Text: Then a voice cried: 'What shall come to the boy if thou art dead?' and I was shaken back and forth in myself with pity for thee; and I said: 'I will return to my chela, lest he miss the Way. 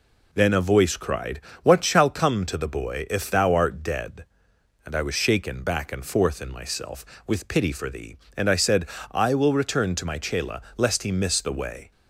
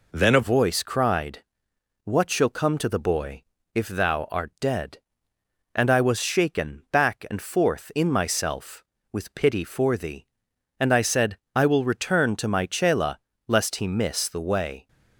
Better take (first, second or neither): first